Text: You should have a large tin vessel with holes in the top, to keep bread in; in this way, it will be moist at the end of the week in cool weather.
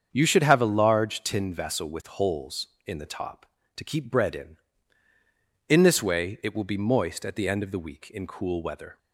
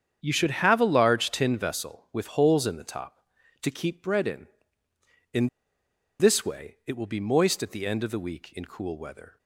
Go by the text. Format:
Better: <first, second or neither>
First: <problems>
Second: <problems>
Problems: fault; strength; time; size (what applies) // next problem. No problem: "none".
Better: first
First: starts louder than the rest; strong; until 1.1 s; 7.5 dB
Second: starts louder than the rest; strong; until 1.2 s; 8 dB // pauses between "in" and "this"; noticeable; at 5.4 s; 0.72 s long